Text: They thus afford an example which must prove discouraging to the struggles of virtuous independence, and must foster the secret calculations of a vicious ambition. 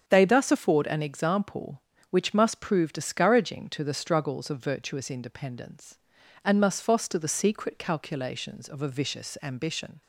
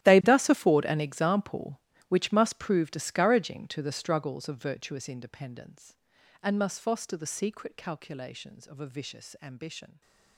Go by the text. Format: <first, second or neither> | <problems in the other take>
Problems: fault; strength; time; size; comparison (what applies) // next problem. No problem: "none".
first | gets quieter; strong; throughout; 18 dB // starts louder than the rest; strong; until 1.0 s; 13.5 dB; strong in the first